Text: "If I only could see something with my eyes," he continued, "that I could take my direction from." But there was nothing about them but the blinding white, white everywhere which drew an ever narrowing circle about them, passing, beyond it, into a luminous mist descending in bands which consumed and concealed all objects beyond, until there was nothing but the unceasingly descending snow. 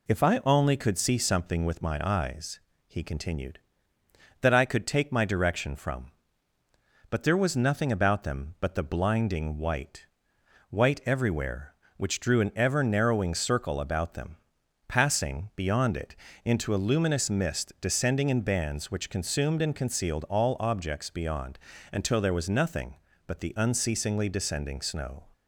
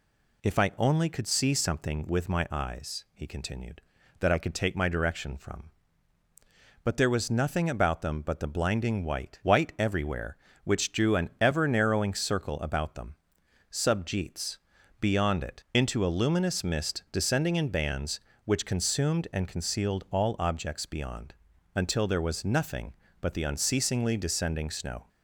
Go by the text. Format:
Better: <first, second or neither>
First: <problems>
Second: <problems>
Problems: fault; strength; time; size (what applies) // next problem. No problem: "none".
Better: first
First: none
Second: says "subjeets" for "passing"; at 13.7 s